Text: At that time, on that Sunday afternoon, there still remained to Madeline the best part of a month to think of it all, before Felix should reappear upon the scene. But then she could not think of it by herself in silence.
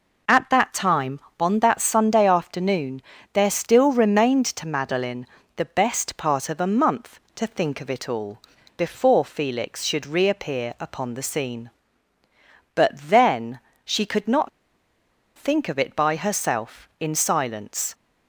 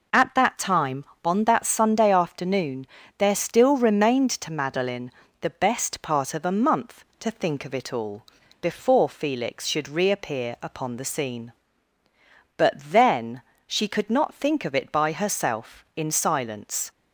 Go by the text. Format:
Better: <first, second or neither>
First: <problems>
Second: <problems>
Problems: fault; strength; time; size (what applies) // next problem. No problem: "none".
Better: second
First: pauses between "Madeline" and "the"; slight; at 5.2 s; 0.28 s long // pauses between "then" and "she"; slight; at 13.5 s; 0.24 s long // pauses between "not" and "think"; noticeable; at 14.4 s; 0.87 s long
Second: pauses between "Madeline" and "the"; slight; at 5.1 s; 0.28 s long // pauses between "then" and "she"; slight; at 13.4 s; 0.24 s long